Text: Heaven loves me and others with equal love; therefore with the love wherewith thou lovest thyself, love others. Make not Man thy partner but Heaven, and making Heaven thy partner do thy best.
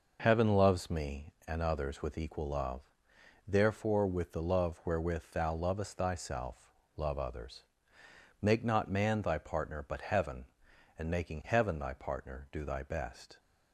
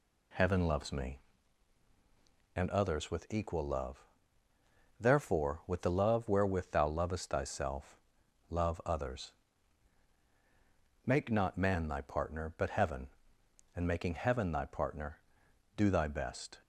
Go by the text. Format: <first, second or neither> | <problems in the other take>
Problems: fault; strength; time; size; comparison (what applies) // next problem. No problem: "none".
neither | none